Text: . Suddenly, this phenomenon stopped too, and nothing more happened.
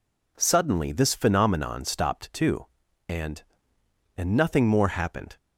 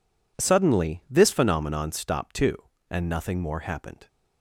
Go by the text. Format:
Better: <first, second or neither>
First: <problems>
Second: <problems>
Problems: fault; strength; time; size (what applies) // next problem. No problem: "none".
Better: second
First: says "and" twice; at 4.1 s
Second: none